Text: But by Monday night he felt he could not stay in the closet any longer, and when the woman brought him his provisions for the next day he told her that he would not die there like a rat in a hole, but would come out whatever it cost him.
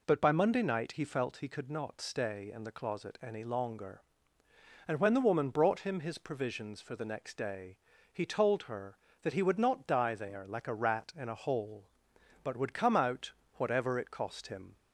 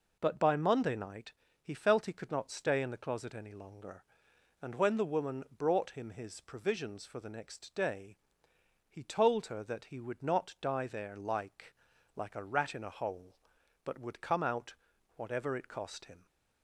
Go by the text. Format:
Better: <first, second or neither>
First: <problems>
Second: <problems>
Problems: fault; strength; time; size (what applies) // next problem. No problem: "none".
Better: first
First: pauses between "day" and "he"; slight; at 7.7 s; 0.34 s long // pauses between "out" and "whatever"; slight; at 13.3 s; 0.26 s long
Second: pauses between "night" and "he"; slight; at 1.3 s; 0.30 s long // pauses between "day" and "he"; noticeable; at 8.1 s; 0.72 s long // says "like" twice; at 12.1 s // pauses between "out" and "whatever"; at 14.7 s; 0.44 s long